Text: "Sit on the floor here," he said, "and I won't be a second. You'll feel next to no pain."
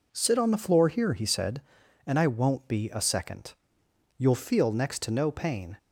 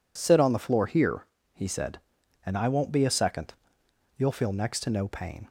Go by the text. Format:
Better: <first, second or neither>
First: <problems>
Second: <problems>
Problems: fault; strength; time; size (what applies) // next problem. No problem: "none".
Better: neither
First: none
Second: none